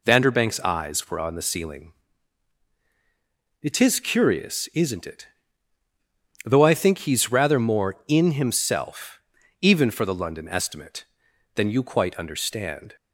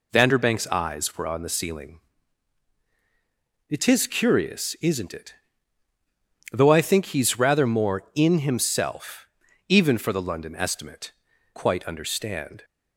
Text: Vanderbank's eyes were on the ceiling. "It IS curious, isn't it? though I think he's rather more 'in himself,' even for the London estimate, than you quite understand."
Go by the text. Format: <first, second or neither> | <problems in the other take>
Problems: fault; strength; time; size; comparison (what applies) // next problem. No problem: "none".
first | skips "than you"; at 11.3 s